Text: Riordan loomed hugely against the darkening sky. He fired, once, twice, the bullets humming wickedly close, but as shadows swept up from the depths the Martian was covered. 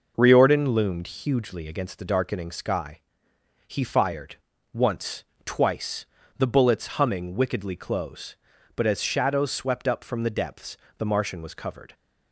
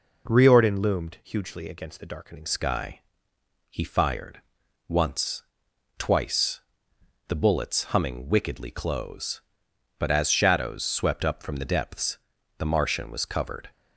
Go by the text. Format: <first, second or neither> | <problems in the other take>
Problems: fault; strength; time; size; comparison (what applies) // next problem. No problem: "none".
first | changes voice at "sky"; from 2.4 s on; 11.2 s long // pauses between "depths" and "the"; at 12.1 s; 0.40 s long; slight in the first